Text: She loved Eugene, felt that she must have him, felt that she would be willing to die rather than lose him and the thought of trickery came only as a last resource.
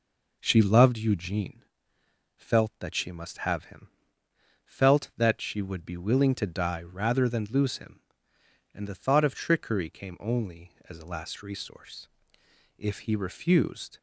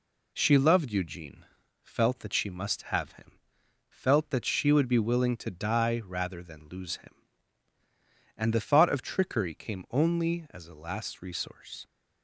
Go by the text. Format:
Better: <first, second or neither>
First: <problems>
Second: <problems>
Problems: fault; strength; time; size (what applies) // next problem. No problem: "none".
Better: second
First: goes on to say "If he refused"; noticeable; from 12.7 s on; 1.2 s long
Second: none